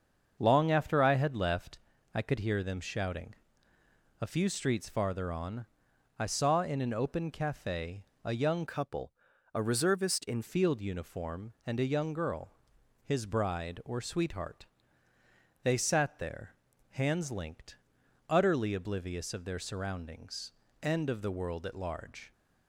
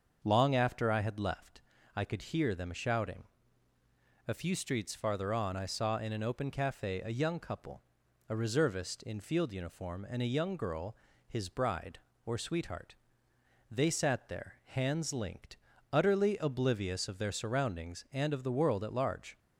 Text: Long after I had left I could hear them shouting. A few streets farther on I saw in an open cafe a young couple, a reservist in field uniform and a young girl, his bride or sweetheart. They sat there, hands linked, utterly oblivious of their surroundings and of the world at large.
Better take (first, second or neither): second